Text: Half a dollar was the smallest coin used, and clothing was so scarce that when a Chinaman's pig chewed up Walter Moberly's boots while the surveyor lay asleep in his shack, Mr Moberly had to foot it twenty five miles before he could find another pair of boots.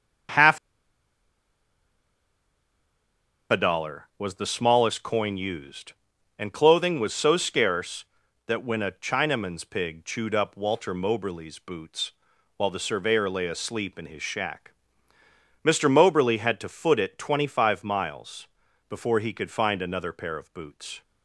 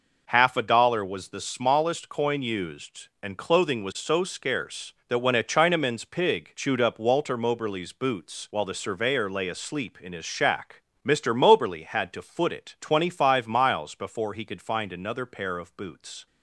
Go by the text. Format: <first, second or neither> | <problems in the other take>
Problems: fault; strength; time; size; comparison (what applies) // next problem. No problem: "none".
second | starts louder than the rest; strong; until 4.3 s; 7.5 dB // pauses between "Half" and "a"; strong; at 0.5 s; 2.9 s long // pauses between "boots" and "while"; at 12.1 s; 0.42 s long // pauses between "miles" and "before"; at 18.4 s; 0.42 s long